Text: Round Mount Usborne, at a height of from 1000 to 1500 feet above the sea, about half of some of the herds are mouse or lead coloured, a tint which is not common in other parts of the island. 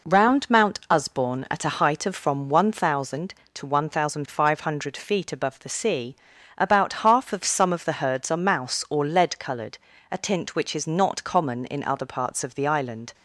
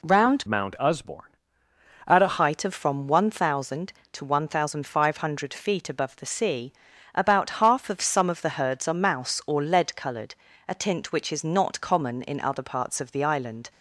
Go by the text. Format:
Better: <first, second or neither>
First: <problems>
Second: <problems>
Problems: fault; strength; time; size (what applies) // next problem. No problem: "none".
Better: first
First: none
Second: changes voice from "Mount" to "a"; from 0.4 to 2.3 s; 1.9 s long